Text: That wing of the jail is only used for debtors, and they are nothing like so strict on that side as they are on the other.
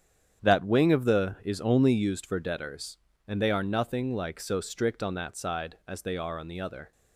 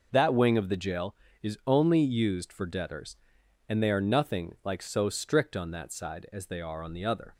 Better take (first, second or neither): second